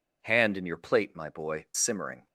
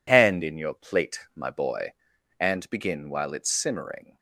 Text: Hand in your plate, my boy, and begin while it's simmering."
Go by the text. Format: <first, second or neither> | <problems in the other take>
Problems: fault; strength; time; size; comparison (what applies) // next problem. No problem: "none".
second | skips "and begin while it's"; at 1.7 s